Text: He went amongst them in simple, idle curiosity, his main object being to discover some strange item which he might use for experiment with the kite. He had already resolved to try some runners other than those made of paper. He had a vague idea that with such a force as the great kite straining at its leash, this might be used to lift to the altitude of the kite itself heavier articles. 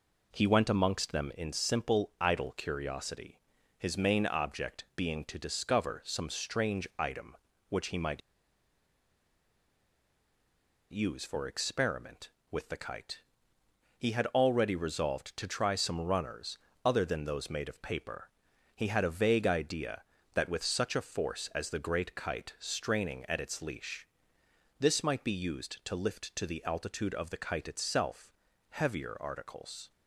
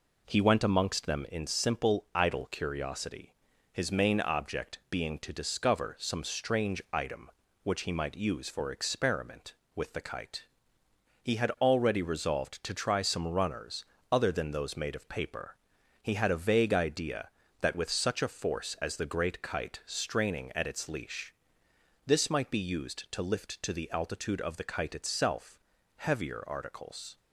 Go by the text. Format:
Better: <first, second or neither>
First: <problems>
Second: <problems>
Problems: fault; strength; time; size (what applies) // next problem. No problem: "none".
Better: second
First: pauses between "might" and "use"; strong; at 8.2 s; 2.7 s long // pauses between "runners" and "other"; slight; at 16.5 s; 0.28 s long // pauses between "itself" and "heavier"; at 28.3 s; 0.38 s long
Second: pauses between "runners" and "other"; slight; at 13.8 s; 0.28 s long // pauses between "itself" and "heavier"; at 25.5 s; 0.38 s long